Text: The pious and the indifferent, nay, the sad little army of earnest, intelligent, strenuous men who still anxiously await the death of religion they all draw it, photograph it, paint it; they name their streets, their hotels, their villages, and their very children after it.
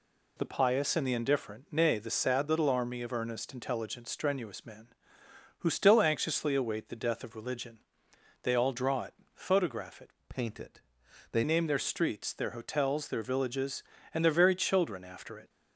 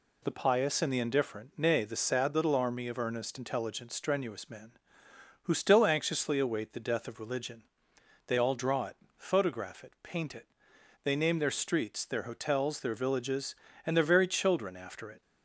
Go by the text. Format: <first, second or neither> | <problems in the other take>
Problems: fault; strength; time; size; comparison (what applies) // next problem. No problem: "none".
second | pauses between "religion" and "they"; noticeable; at 7.7 s; 0.64 s long; noticeable in the second // changes voice from "paint" to "they"; from 10.2 to 11.4 s; 1.2 s long